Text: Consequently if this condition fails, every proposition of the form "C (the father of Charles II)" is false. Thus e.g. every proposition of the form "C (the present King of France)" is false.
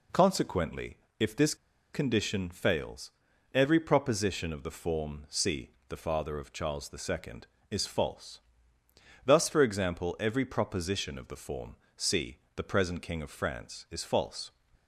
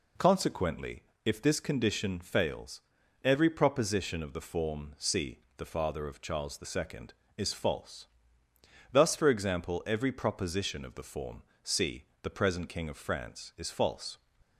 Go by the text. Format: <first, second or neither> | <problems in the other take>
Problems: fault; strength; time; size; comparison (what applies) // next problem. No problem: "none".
second | pauses between "Consequently" and "if"; slight; at 0.9 s; 0.22 s long; slight in the second // pauses between "this" and "condition"; at 1.5 s; 0.38 s long // pauses between "form" and "C"; slight; at 11.7 s; 0.22 s long; slight in the second